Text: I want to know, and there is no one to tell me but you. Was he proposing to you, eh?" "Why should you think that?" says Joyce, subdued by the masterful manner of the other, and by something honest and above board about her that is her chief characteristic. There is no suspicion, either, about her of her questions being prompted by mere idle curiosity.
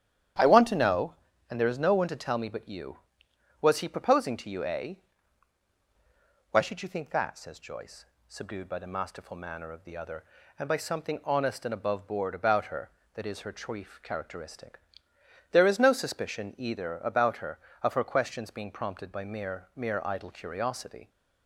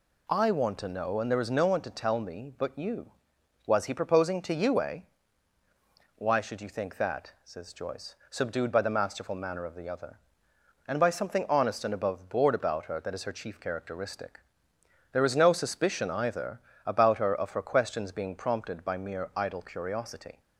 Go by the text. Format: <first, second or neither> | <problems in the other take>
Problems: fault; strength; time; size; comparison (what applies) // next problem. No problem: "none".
second | starts louder than the rest; strong; until 1.7 s; 10 dB // says "mere" twice; at 19.7 s